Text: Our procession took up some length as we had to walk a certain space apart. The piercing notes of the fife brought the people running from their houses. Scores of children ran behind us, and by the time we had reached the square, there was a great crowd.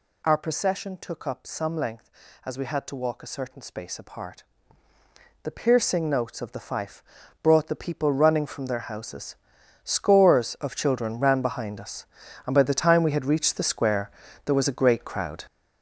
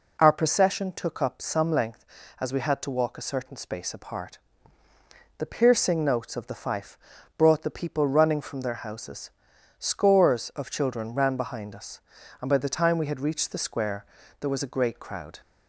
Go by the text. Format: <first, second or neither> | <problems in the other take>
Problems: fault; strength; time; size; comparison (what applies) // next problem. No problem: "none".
second | gets louder; strong; throughout; 9.5 dB // pauses between "fife" and "brought"; at 7.0 s; 0.40 s long; also in the second